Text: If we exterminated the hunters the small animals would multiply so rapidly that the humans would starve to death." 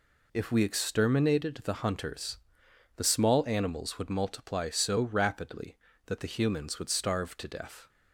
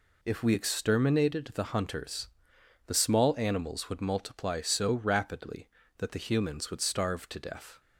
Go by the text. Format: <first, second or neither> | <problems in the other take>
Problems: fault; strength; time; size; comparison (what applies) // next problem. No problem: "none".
neither | pauses between "hunters" and "the"; noticeable; the same in both